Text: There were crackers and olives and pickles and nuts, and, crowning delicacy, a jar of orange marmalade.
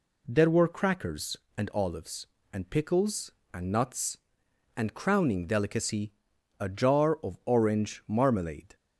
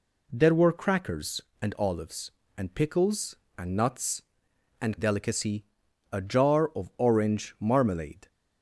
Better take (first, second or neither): first